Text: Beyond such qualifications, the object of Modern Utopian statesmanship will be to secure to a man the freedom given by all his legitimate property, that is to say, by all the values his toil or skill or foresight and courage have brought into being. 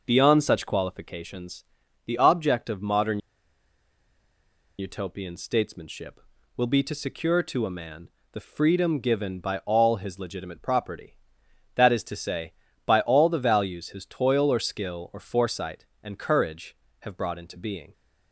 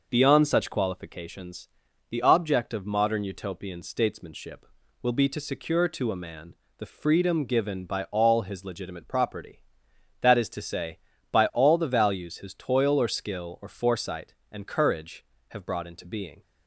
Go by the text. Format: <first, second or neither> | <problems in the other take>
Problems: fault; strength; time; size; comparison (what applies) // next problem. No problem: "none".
second | pauses between "Modern" and "Utopian"; strong; at 3.1 s; 1.5 s long // pauses between "man" and "the"; slight; at 8.0 s; 0.24 s long; slight in the second